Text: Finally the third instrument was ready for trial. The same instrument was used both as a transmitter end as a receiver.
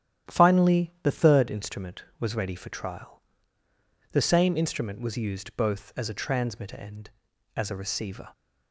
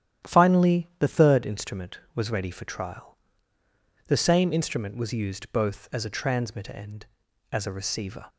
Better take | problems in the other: neither | starts louder than the rest; strong; the same in both

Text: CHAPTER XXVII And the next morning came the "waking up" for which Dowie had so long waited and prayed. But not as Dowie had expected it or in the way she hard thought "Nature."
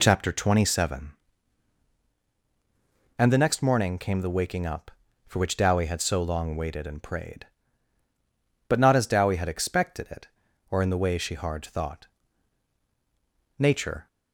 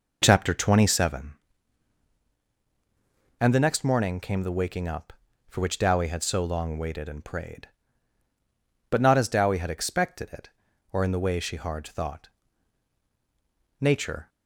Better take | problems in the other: first | starts louder than the rest; noticeable; until 1.1 s; 5 dB // pauses between "thought" and "Nature"; strong; at 12.2 s; 1.5 s long; strong in the first

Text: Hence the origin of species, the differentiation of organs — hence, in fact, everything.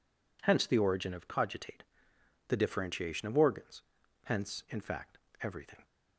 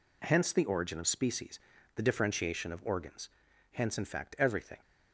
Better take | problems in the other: second | says "cogitate" for "species"; at 1.2 s

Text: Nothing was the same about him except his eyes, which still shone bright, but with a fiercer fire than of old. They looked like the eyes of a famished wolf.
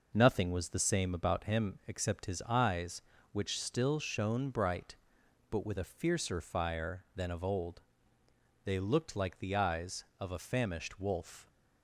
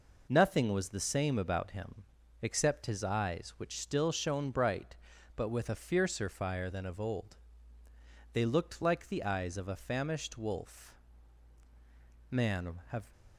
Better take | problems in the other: first | pauses between "him" and "except"; at 2.0 s; 0.38 s long // goes on to say "Man have"; noticeable; from 12.3 s on; 0.80 s long

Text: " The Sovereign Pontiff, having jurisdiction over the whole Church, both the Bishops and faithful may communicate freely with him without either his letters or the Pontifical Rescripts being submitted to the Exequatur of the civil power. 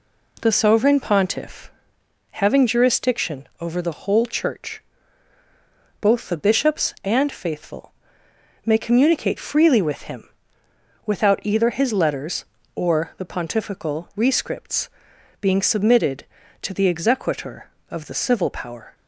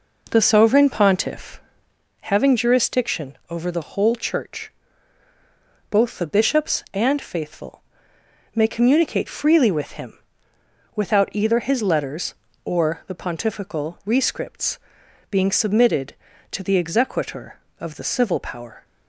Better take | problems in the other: first | starts louder than the rest; noticeable; until 2.1 s; 4.5 dB // pauses between "faithful" and "may"; noticeable; at 7.8 s; 0.72 s long; noticeable in the first // pauses between "him" and "without"; noticeable; at 10.1 s; 0.76 s long; noticeable in the first // pauses between "Rescripts" and "being"; noticeable; at 14.7 s; 0.54 s long; noticeable in the first

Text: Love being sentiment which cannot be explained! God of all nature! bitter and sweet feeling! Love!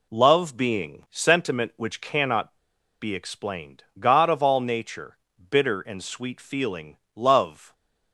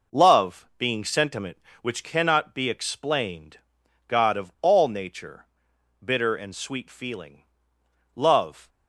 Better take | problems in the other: second | pauses between "cannot" and "be"; at 2.5 s; 0.45 s long

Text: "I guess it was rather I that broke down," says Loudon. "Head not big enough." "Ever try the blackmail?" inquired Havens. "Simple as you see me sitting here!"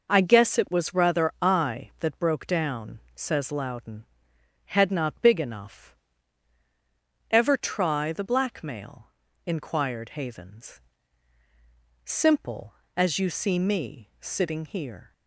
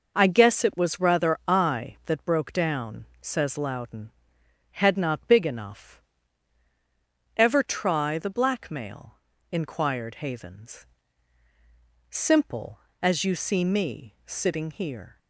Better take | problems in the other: neither | none

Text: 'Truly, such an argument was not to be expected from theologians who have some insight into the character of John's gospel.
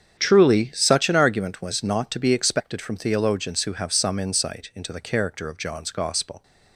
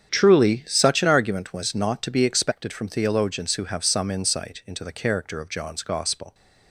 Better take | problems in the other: neither | starts louder than the rest; strong; the same in both

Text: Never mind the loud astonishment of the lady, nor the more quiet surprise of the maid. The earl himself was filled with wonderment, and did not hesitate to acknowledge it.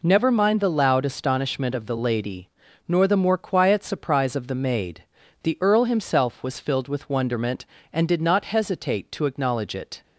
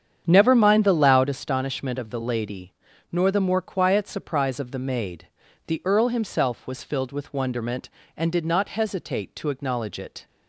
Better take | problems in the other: first | starts louder than the rest; strong; until 1.3 s; 8.5 dB

